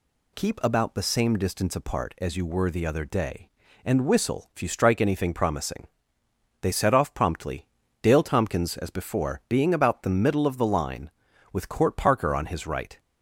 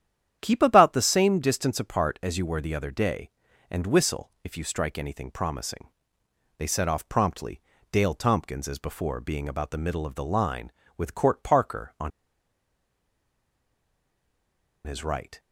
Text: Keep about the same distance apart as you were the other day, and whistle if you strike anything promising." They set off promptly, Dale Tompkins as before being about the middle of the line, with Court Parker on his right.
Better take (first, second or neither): first